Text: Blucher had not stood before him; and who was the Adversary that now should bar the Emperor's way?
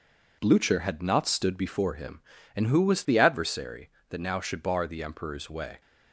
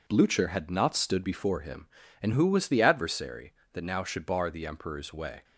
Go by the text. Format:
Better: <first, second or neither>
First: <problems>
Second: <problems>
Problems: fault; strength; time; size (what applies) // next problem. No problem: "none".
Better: neither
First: none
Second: none